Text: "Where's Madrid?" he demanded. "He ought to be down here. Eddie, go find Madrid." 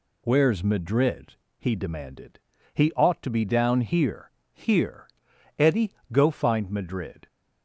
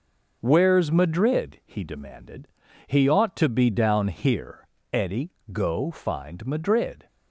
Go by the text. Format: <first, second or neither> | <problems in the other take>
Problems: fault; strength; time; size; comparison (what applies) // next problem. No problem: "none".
second | says "here" twice; at 4.5 s